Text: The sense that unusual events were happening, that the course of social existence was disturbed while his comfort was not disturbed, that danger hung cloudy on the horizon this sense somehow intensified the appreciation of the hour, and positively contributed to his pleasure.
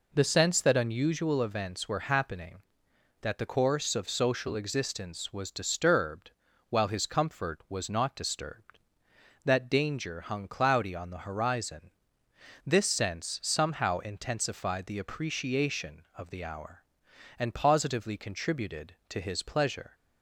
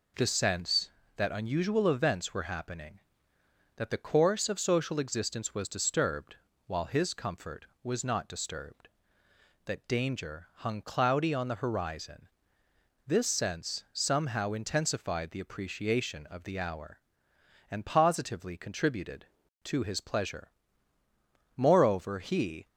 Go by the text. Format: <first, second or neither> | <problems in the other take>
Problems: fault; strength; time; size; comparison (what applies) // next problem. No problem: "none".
first | pauses between "disturbed" and "while"; slight; at 6.3 s; 0.30 s long; slight in the first // pauses between "horizon" and "this"; noticeable; at 12.2 s; 0.76 s long; noticeable in the first // goes on to say "Moreover he"; noticeable; from 21.5 s on; 1.1 s long